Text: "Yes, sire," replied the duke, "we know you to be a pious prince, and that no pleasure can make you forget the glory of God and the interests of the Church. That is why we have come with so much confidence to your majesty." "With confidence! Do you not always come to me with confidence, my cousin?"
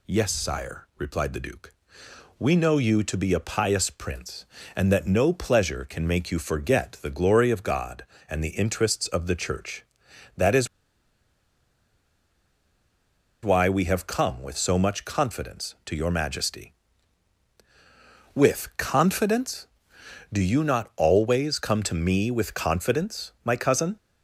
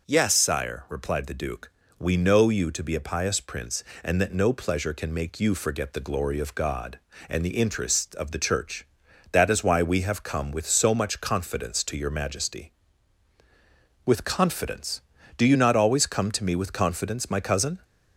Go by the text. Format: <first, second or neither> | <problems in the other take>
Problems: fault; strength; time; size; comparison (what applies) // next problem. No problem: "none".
second | pauses between "is" and "why"; strong; at 10.6 s; 2.7 s long